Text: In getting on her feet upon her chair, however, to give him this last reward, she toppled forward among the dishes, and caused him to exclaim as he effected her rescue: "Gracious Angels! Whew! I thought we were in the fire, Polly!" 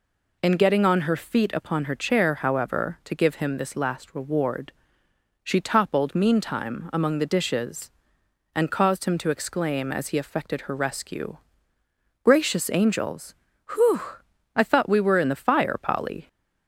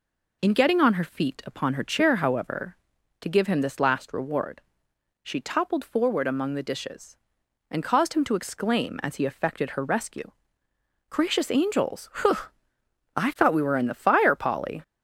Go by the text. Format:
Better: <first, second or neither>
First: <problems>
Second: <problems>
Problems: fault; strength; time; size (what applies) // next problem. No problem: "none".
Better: second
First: says "meantime" for "forward"; at 6.1 s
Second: none